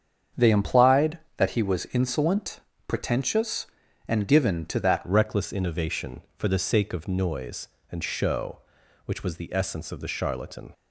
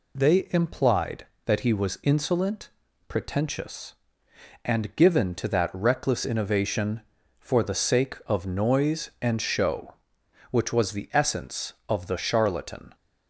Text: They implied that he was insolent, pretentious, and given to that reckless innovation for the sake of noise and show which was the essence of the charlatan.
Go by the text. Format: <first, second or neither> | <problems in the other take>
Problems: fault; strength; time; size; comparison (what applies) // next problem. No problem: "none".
second | starts louder than the rest; strong; until 1.5 s; 7.5 dB // changes voice at "reckless"; from 5.0 s on; 5.7 s long